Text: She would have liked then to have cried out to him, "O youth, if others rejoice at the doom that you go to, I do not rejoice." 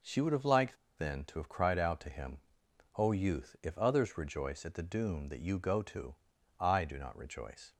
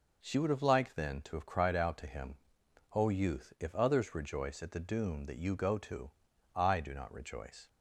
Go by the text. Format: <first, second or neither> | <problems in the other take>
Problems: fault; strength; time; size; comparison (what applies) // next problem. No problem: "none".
second | pauses between "liked" and "then"; slight; at 0.7 s; 0.23 s long